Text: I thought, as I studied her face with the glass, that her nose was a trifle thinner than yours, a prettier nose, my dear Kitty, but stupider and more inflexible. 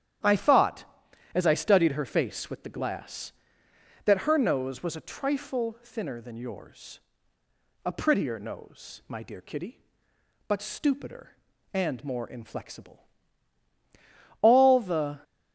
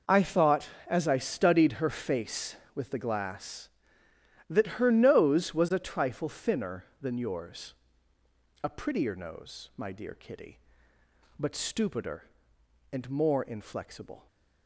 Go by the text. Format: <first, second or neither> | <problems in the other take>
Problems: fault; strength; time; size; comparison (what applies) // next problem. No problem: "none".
second | starts louder than the rest; strong; until 1.7 s; 10.5 dB // goes on to say "All the"; noticeable; from 14.4 s on; 0.80 s long